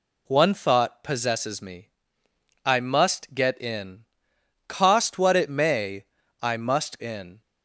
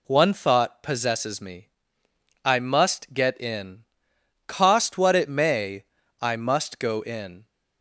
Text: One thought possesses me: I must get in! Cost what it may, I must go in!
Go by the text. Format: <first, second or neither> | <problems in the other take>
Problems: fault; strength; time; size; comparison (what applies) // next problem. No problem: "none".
second | skips "go"; at 6.9 s